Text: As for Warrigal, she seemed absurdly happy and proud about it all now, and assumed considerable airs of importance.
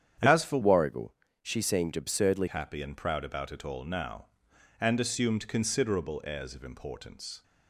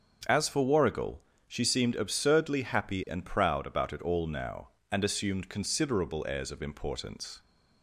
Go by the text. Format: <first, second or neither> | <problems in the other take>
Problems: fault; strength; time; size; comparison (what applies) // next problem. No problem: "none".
second | starts louder than the rest; strong; until 1.5 s; 9 dB; also in the second // changes voice from "Warrigal" to "absurdly"; from 0.6 to 2.4 s; 1.8 s long